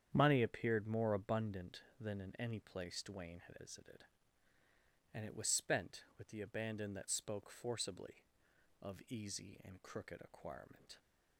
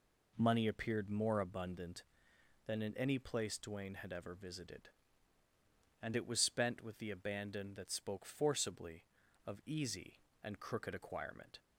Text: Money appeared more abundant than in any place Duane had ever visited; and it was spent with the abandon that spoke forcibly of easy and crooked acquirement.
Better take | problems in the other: second | starts louder than the rest; strong; until 1.1 s; 8.5 dB // skips "ever"; at 3.5 s

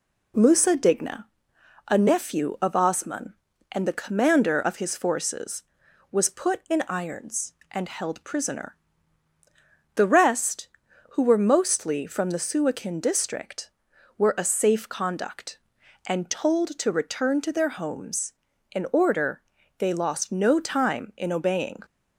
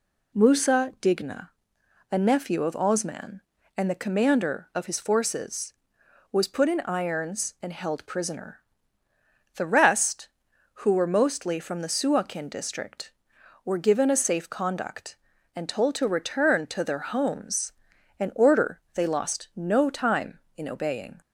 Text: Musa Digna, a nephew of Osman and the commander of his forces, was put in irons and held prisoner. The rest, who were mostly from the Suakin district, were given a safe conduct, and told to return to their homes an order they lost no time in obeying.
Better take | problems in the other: second | skips "given"; at 14.3 s // pauses between "homes" and "an"; at 18.3 s; 0.40 s long; noticeable in the second // pauses between "order" and "they"; at 19.4 s; 0.38 s long

